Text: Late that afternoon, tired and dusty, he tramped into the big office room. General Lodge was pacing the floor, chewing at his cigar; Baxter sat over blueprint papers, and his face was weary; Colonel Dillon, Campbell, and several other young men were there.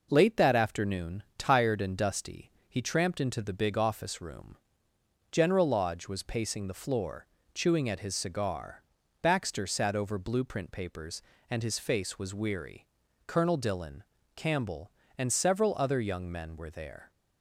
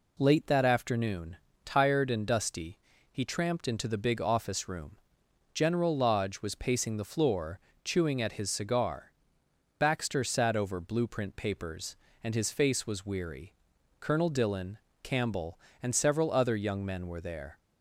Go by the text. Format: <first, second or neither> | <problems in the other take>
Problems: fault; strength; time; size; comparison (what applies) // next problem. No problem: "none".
neither | none